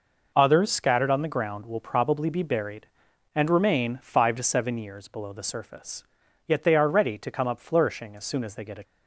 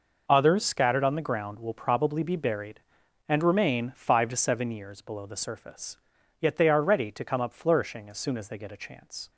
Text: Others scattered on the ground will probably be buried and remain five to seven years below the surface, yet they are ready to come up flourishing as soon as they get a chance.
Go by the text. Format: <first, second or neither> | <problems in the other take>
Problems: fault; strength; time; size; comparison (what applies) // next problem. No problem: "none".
second | stops before "chance"; at 8.8 s